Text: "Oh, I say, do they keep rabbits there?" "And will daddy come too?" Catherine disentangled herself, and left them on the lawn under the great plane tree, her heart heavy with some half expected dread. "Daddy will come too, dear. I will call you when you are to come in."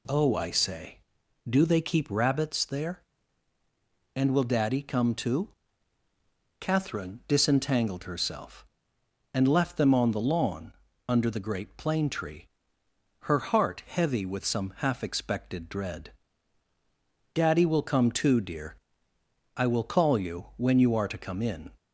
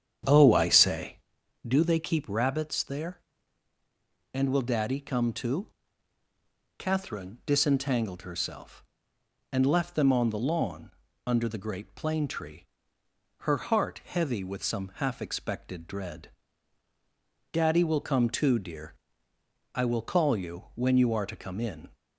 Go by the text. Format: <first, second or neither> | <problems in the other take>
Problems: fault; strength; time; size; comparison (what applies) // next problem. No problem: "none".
first | starts louder than the rest; strong; until 1.3 s; 8.5 dB // pauses between "lawn" and "under"; slight; at 10.9 s; 0.34 s long; slight in the first